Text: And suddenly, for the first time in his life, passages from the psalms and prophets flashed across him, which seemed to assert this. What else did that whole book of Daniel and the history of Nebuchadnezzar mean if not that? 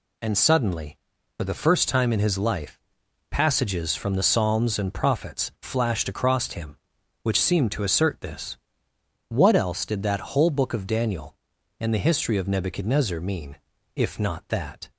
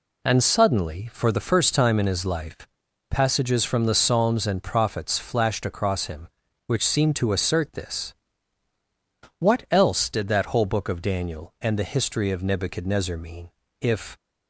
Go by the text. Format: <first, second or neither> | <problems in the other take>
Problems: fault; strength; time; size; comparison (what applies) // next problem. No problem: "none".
first | pauses between "mean" and "if"; slight; at 13.4 s; 0.30 s long; also in the first // stops before "not that"; at 14.1 s